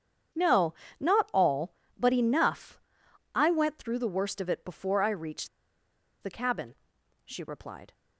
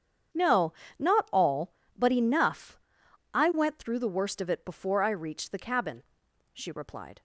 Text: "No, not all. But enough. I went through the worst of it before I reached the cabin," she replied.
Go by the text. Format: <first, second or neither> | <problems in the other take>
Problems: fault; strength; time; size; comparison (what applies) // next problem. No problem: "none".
second | starts louder than the rest; strong; until 1.6 s; 8 dB; strong in the second // pauses between "reached" and "the"; noticeable; at 5.4 s; 0.73 s long